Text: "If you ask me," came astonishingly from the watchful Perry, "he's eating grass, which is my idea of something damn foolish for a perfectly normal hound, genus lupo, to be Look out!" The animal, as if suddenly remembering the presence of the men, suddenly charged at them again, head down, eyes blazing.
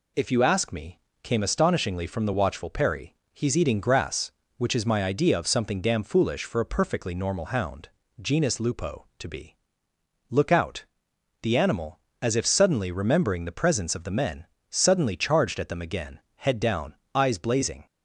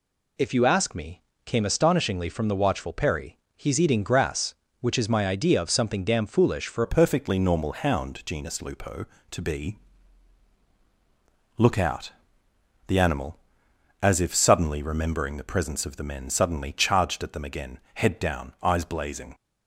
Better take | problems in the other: first | changes voice at "a"; from 6.8 s on; 12.5 s long // pauses between "be" and "Look"; strong; at 9.7 s; 1.8 s long; noticeable in the first

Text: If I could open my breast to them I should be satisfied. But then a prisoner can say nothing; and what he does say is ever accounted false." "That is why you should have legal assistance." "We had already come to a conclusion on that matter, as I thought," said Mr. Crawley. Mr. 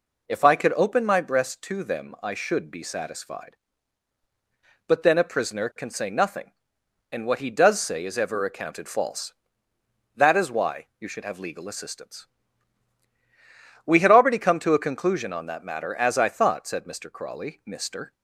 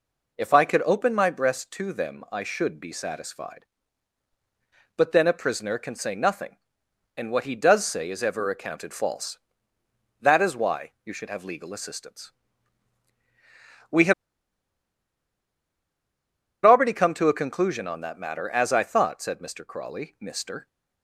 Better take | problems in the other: first | pauses between "why" and "you"; slight; at 10.9 s; 0.16 s long; slight in the first // pauses between "had" and "already"; strong; at 14.1 s; 2.5 s long

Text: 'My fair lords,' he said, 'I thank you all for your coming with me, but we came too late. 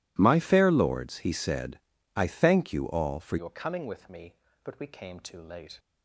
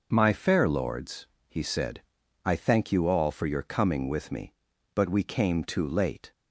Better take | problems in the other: second | changes voice at "your"; from 3.3 s on; 2.4 s long

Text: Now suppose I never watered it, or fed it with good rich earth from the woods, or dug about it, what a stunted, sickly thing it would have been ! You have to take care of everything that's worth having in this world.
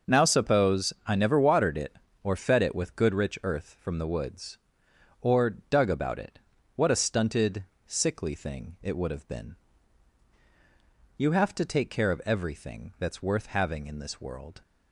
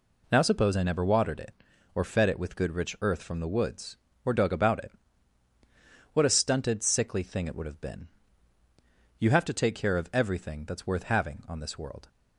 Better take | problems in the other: first | says "on" for "in"; at 11.4 s

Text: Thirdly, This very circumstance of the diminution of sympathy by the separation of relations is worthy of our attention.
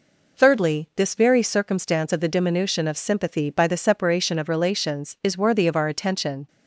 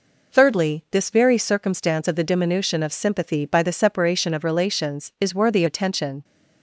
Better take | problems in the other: first | skips "of our"; at 5.6 s

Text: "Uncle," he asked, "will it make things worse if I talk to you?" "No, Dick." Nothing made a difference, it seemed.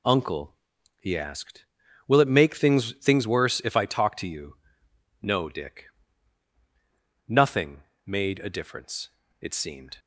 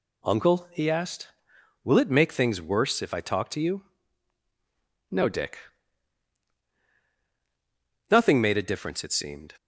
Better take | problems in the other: second | says "things" twice; at 3.0 s // pauses between "Nothing" and "made"; slight; at 7.8 s; 0.24 s long

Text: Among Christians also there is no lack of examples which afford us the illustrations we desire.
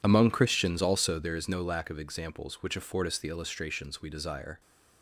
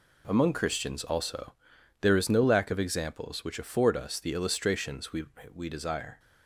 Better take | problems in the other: first | pauses between "also" and "there"; noticeable; at 1.5 s; 0.50 s long // says "we" twice; at 5.5 s

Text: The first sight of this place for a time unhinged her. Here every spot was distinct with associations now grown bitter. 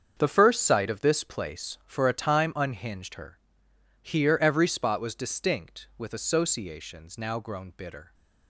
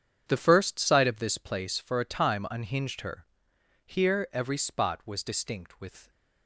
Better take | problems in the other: first | starts louder than the rest; strong; until 1.2 s; 8 dB; strong in the first // stops before "associations now grown bitter"; at 6.0 s

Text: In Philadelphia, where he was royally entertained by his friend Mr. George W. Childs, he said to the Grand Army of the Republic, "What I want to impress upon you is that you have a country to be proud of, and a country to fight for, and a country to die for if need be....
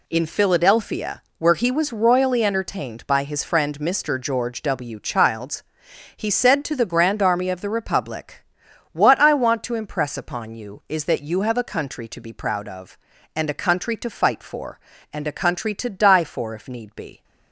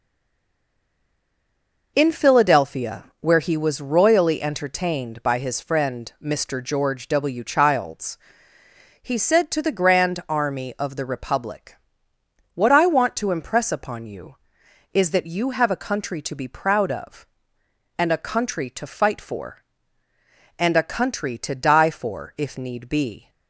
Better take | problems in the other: first | stays silent before the first word; noticeable; until 1.9 s; 1.9 s long

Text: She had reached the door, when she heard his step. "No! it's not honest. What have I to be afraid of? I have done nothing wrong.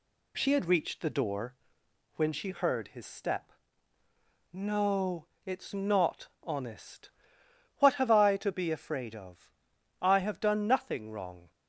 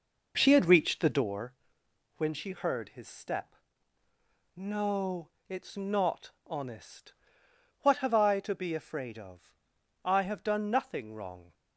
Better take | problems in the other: first | starts louder than the rest; noticeable; until 1.3 s; 5 dB

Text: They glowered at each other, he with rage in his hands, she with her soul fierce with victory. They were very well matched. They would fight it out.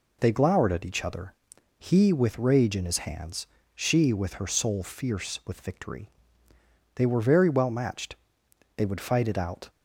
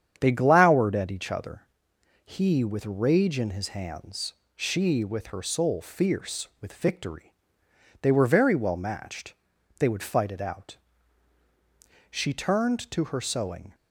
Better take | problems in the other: first | starts louder than the rest; strong; until 1.2 s; 8.5 dB // goes on to say "She turned to her sewing"; from 12.1 s on; 1.6 s long

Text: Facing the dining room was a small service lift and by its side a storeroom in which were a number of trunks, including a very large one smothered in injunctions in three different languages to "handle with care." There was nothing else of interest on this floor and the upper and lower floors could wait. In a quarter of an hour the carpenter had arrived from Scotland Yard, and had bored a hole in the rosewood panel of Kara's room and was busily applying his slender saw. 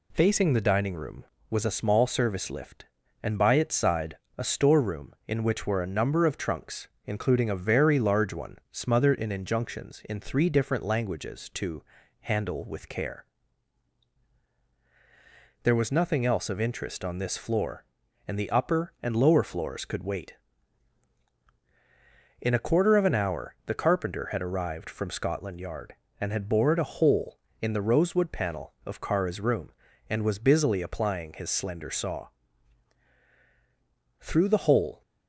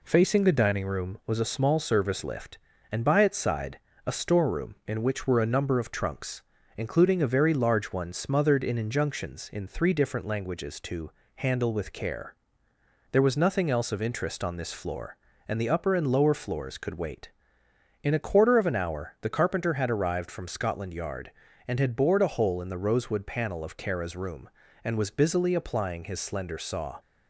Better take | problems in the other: second | pauses between "side" and "a"; slight; at 4.1 s; 0.20 s long; slight in the second // pauses between "one" and "smothered"; slight; at 8.5 s; 0.16 s long // pauses between "to" and "handle"; at 11.8 s; 0.40 s long; slight in the second // goes on to say "Through the hole"; noticeable; from 34.1 s on; 0.82 s long

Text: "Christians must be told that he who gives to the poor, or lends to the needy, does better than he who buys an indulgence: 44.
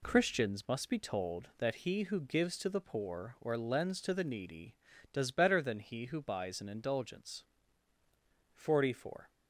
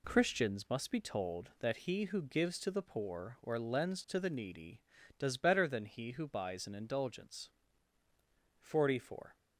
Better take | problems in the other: neither | none

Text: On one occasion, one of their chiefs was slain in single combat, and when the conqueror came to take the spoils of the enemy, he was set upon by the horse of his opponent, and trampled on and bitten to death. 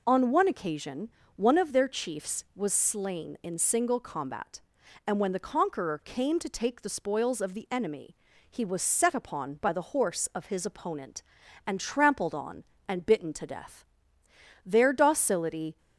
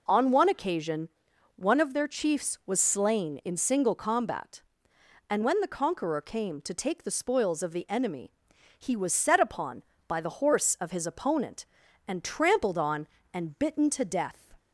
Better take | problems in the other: second | goes on to say "Their docility"; noticeable; from 14.6 s on; 1.1 s long

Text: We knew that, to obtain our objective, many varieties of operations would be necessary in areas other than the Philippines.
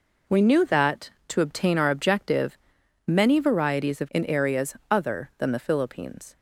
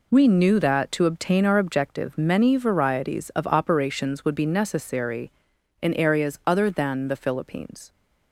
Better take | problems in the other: second | skips "operations would be necessary"; at 4.0 s // pauses between "areas" and "other"; slight; at 4.7 s; 0.16 s long

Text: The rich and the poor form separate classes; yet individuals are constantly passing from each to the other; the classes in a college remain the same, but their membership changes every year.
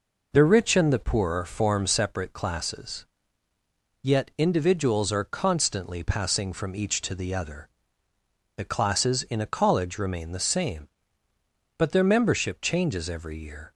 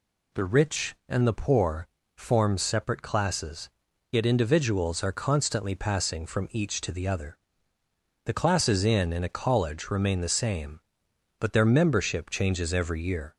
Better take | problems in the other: first | pauses between "poor" and "form"; slight; at 1.8 s; 0.30 s long // says "in" twice; at 9.1 s

